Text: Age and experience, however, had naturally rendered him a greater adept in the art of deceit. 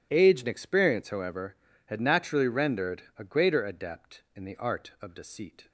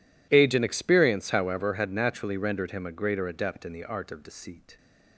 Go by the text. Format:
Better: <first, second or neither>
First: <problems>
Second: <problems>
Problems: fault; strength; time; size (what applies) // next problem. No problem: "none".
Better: second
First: skips "him"; at 3.0 s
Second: none